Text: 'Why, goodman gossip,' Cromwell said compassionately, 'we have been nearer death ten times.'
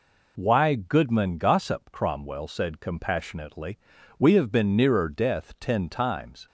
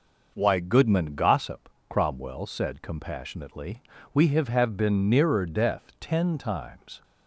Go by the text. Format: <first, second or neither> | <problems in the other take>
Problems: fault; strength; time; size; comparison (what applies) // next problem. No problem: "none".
first | says "have" twice; at 4.4 s